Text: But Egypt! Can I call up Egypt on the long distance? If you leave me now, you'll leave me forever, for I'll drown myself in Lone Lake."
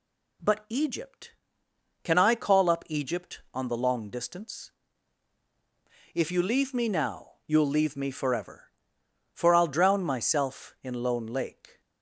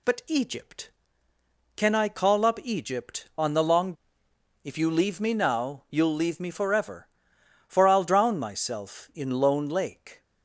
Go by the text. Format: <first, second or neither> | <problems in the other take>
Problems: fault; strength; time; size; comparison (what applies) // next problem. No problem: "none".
first | skips "distance"; at 4.2 s